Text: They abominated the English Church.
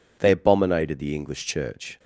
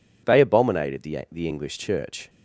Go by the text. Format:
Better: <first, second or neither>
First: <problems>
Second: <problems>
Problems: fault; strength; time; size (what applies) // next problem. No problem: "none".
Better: first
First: none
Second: says "the" twice; at 1.3 s